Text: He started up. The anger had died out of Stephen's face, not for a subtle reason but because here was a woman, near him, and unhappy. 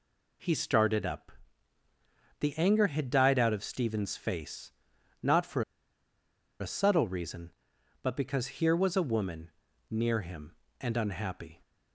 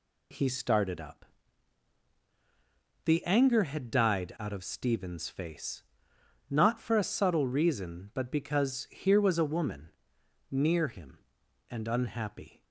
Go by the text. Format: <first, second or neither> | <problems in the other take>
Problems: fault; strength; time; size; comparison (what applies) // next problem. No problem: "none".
second | pauses between "for" and "a"; at 5.6 s; 0.99 s long